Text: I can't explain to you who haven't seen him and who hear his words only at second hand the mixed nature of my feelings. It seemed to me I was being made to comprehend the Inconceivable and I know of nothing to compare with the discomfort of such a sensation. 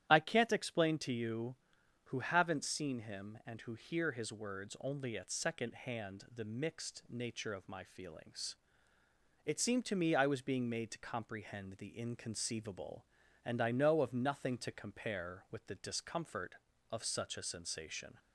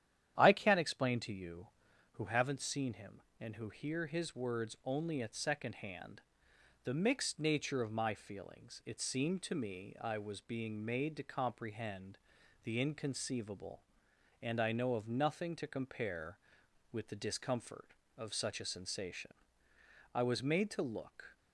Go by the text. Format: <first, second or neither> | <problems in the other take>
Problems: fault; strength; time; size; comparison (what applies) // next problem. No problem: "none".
first | starts louder than the rest; strong; until 1.4 s; 10.5 dB; strong in the first // pauses between "hand" and "the"; noticeable; at 6.2 s; 0.64 s long // pauses between "comprehend" and "the"; noticeable; at 12.1 s; 0.46 s long // goes on to say "I was made to look"; noticeable; from 20.1 s on; 1.2 s long